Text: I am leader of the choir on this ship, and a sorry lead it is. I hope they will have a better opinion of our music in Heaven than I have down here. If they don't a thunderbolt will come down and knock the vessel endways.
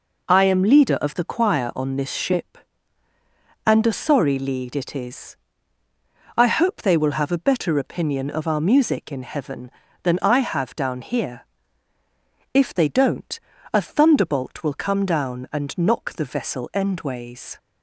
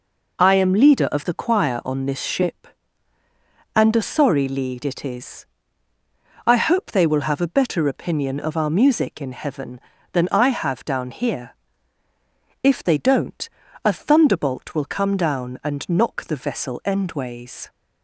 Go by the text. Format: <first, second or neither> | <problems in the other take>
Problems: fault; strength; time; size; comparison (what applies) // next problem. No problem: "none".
neither | pauses between "don't" and "a"; the same in both